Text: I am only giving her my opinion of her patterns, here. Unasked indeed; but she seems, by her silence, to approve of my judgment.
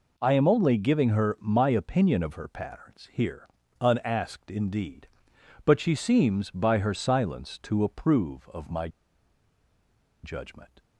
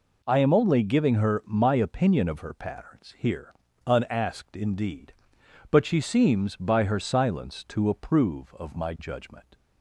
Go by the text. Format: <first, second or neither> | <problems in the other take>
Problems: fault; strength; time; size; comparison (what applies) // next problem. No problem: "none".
second | pauses between "my" and "judgment"; strong; at 8.8 s; 1.3 s long